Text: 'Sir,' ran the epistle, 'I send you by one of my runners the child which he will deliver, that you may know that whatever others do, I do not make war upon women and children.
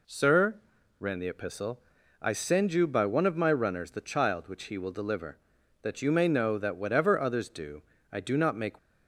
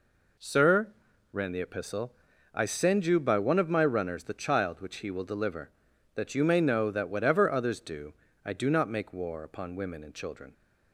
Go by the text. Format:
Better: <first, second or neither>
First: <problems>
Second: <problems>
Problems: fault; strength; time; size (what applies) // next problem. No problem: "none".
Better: second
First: stops before "war upon women and children"; at 8.7 s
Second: none